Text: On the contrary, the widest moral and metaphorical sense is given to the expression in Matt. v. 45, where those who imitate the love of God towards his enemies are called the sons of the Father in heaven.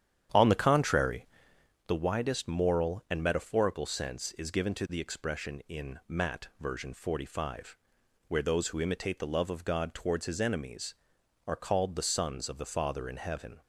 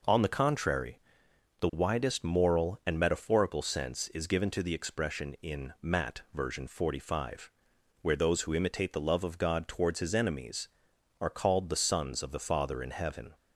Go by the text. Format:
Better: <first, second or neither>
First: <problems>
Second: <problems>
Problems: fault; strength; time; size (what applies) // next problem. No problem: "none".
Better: second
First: starts louder than the rest; strong; until 1.8 s; 9.5 dB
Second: none